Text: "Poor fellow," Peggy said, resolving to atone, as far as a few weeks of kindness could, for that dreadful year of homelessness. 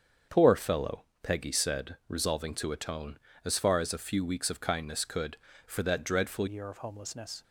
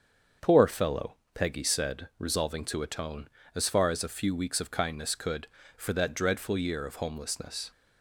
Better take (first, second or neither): second